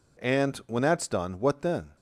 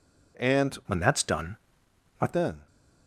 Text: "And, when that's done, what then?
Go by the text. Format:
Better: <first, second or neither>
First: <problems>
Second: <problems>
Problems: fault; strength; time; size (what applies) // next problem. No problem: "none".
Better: first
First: none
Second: changes voice from "when" to "what"; from 0.8 to 2.3 s; 1.5 s long